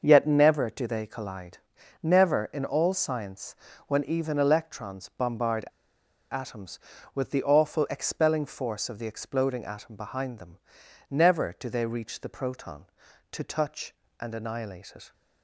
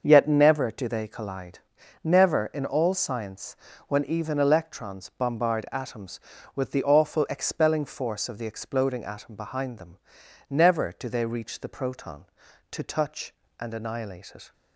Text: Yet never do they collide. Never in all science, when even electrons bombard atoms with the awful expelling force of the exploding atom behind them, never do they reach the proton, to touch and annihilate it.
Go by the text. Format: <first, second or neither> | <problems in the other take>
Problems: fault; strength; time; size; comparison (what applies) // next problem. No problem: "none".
second | starts louder than the rest; until 1.0 s; 6.5 dB; also in the second // pauses between "bombard" and "atoms"; noticeable; at 5.6 s; 0.66 s long